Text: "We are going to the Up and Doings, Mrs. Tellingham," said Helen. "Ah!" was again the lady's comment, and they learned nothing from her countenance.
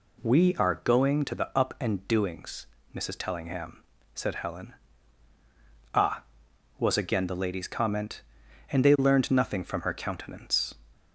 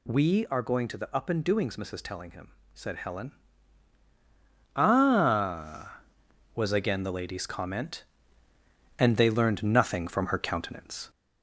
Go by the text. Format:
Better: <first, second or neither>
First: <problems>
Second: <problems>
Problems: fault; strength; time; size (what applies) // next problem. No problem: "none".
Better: first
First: none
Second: gets louder; slight; throughout; 2.5 dB